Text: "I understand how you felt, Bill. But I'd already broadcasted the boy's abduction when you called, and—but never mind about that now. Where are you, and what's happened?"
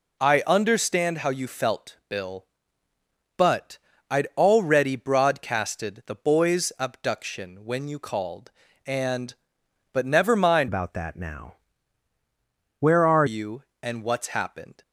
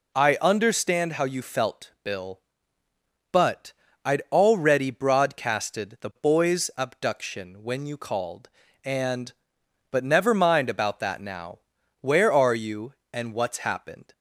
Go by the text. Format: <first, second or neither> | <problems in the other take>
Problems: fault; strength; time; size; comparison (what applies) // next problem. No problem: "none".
second | pauses between "But" and "I'd"; slight; at 3.7 s; 0.32 s long; slight in the second // changes voice from "about" to "are"; from 10.6 to 13.2 s; 2.6 s long